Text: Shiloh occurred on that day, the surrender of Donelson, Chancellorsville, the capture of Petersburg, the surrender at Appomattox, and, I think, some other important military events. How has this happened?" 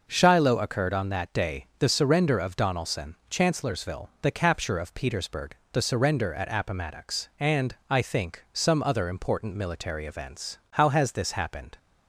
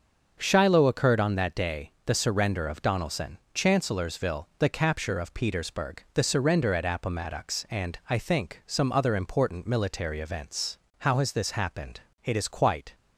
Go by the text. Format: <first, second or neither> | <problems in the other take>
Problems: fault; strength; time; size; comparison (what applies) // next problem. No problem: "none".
first | starts louder than the rest; until 1.4 s; 6.5 dB // goes on to say "It is quite"; noticeable; from 12.2 s on; 0.72 s long